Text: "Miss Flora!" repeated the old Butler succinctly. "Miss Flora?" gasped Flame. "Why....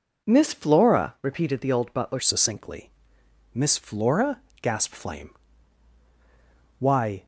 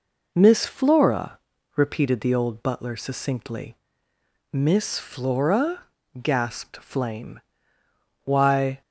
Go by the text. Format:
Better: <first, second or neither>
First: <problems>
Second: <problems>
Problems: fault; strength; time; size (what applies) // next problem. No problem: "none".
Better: second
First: changes voice at "succinctly"; from 2.1 s on; 5.1 s long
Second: none